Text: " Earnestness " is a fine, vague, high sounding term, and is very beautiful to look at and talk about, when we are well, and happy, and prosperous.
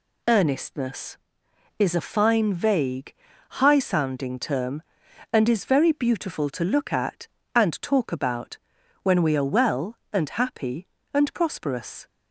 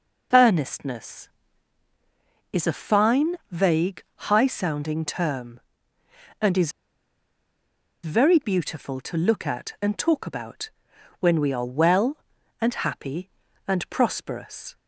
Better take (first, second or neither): first